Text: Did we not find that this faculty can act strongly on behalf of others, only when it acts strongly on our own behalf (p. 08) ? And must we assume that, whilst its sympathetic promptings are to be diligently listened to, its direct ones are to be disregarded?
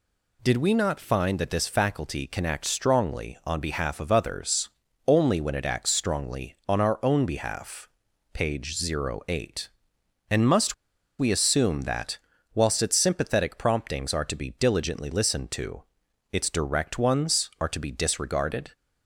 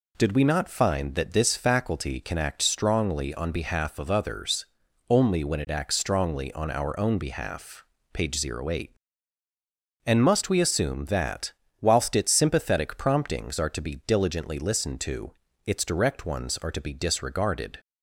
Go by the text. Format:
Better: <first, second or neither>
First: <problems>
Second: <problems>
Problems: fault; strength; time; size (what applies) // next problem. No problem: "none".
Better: second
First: pauses between "must" and "we"; at 10.7 s; 0.44 s long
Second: none